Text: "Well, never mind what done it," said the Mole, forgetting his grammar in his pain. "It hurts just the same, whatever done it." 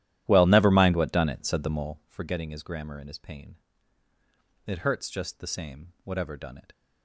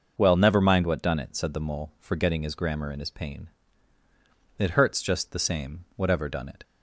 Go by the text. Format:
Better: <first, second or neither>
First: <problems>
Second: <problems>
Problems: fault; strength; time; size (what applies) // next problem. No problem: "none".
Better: second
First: starts louder than the rest; strong; until 2.1 s; 13 dB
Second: none